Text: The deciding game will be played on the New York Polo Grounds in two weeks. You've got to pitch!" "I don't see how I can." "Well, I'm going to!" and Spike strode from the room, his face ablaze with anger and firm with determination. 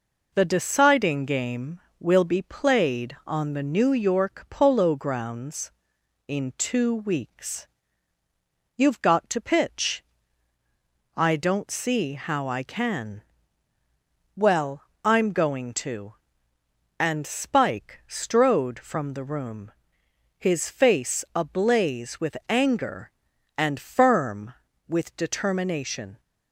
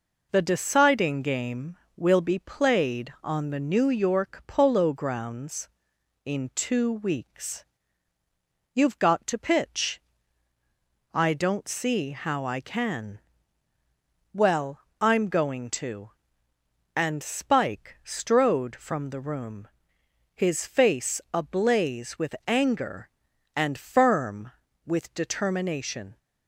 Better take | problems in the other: neither | none

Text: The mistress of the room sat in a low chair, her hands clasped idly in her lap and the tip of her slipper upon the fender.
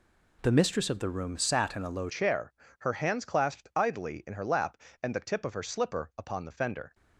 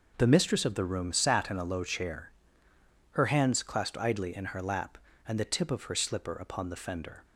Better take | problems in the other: second | changes voice at "chair"; from 2.0 s on; 4.9 s long

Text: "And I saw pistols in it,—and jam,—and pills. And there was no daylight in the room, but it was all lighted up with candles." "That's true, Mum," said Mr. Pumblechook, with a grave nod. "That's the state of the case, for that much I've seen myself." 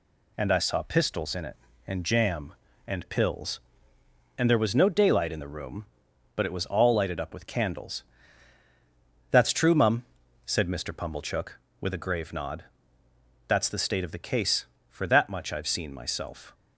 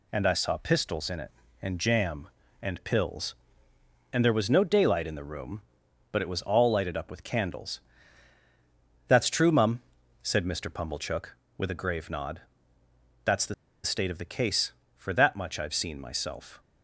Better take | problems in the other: first | pauses between "the" and "state"; slight; at 13.5 s; 0.30 s long

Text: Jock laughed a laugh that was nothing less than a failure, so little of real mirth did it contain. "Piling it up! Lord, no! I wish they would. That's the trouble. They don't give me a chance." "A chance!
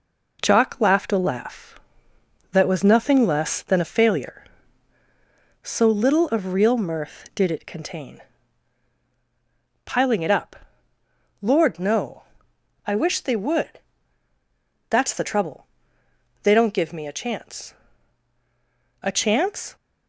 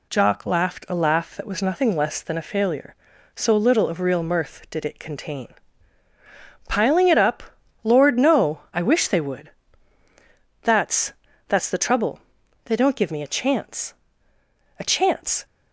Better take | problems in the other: first | says "That's" twice; at 11.4 s

